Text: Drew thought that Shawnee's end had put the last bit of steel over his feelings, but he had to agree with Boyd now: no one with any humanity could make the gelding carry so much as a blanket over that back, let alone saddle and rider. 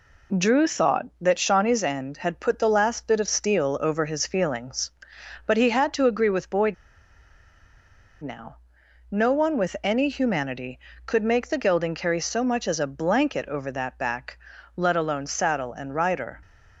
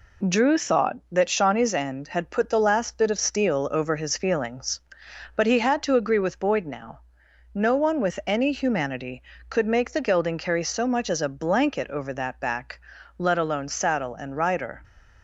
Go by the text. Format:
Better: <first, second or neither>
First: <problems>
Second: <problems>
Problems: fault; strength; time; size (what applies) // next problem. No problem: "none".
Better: second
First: pauses between "Boyd" and "now"; strong; at 6.7 s; 1.4 s long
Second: none